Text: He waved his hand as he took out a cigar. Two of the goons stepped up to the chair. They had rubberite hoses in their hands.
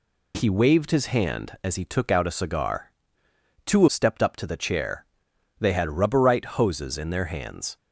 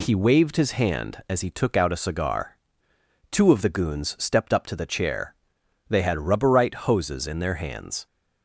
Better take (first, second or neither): second